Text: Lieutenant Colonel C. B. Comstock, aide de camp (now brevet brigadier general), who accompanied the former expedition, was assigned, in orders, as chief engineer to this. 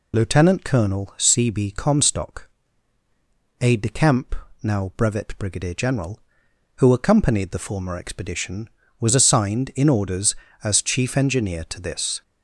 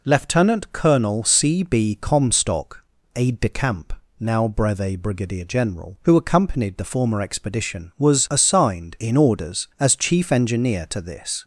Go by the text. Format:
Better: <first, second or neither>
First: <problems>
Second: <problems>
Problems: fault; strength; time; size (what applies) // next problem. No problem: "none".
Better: second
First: loses the start of "Lieutenant"; at 0.1 s; 40 ms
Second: none